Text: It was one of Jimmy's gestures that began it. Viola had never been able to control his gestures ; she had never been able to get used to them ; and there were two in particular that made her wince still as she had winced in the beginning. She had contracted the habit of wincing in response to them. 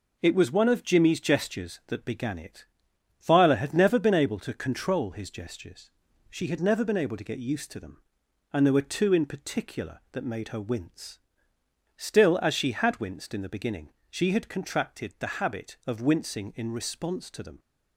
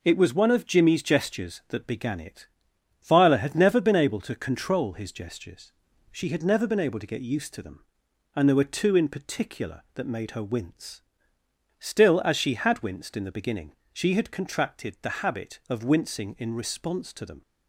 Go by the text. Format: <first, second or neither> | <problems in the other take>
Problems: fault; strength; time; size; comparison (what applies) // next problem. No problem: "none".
neither | pauses between "wince" and "still"; noticeable; the same in both